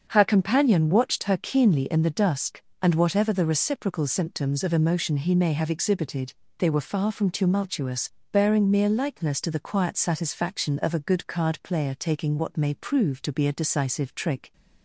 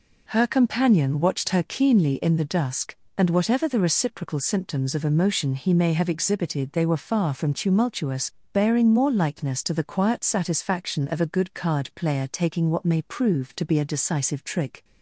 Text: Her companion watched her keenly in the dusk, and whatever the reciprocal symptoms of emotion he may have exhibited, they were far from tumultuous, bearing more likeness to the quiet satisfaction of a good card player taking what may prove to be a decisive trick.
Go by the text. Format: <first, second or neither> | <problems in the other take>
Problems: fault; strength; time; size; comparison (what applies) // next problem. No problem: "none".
second | starts louder than the rest; until 1.1 s; 7 dB // says "mere" for "more"; at 8.7 s